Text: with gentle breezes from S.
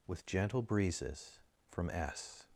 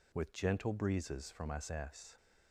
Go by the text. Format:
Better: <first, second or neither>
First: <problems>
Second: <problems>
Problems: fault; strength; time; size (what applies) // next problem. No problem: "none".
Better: first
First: none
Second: says "S" twice; at 1.7 s